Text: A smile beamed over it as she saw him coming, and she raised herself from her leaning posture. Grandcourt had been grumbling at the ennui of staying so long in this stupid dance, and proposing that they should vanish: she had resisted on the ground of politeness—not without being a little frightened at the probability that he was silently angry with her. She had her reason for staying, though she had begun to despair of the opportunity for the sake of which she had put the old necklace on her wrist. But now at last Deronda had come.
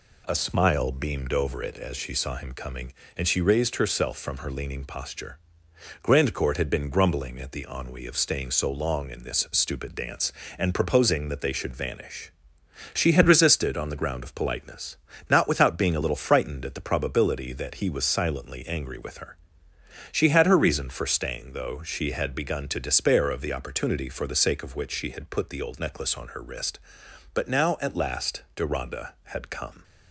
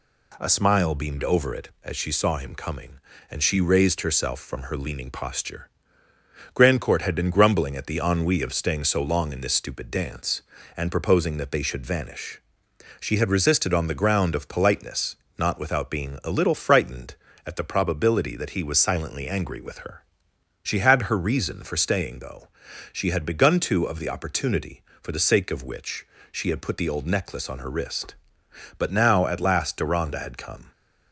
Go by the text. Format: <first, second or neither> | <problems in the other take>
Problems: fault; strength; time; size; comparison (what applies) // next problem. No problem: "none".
first | pauses between "though" and "she"; at 22.4 s; 0.42 s long // skips "despair"; at 23.8 s // pauses between "which" and "she"; slight; at 26.0 s; 0.24 s long